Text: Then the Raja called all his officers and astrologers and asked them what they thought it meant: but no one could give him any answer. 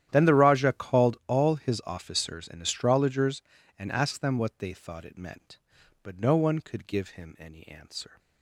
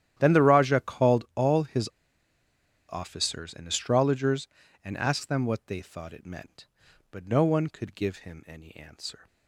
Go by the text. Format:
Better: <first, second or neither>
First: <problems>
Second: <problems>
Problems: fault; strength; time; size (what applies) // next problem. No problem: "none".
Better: first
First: starts louder than the rest; strong; until 1.1 s; 11.5 dB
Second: starts louder than the rest; strong; until 1.1 s; 11.5 dB // pauses between "his" and "officers"; at 1.8 s; 1.0 s long